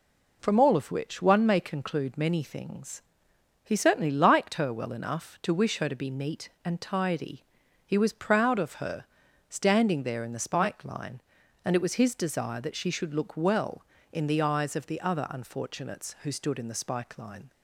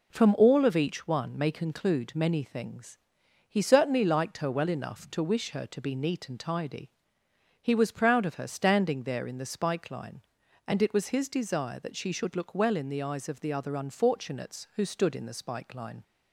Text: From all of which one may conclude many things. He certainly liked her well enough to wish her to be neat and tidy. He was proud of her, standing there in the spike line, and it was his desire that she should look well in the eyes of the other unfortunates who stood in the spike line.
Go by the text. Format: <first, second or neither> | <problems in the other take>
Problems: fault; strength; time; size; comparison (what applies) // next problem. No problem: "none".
first | says "each" for "which"; at 0.7 s